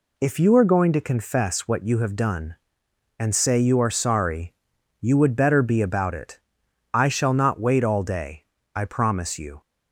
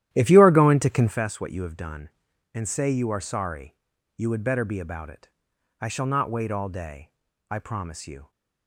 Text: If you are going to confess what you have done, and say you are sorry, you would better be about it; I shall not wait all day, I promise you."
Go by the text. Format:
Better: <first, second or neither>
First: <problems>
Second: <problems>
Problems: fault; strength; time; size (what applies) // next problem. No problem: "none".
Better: first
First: none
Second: starts louder than the rest; strong; until 1.2 s; 12.5 dB